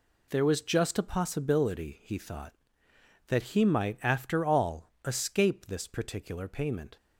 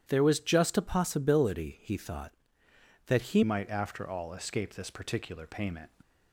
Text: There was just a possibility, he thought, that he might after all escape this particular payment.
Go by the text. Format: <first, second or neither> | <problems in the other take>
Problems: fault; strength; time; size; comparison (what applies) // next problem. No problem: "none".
first | starts louder than the rest; strong; until 1.1 s; 10.5 dB // changes voice at "might"; from 3.4 s on; 2.4 s long